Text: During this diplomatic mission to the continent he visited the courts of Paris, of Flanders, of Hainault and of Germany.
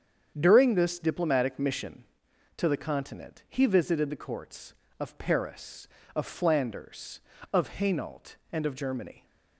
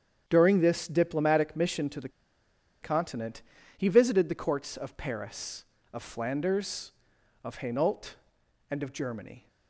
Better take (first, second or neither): first